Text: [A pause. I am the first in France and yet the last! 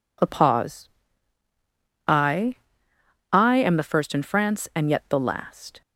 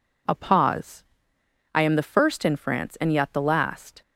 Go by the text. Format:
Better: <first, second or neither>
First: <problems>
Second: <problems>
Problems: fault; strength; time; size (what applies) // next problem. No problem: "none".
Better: second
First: says "I" twice; at 3.3 s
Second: none